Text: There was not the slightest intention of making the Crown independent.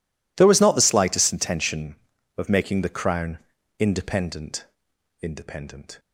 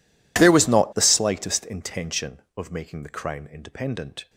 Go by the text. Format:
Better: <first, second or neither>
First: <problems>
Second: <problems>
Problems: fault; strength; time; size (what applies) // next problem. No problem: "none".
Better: second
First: pauses between "Crown" and "independent"; at 3.3 s; 0.42 s long // says "independent" twice; at 5.2 s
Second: none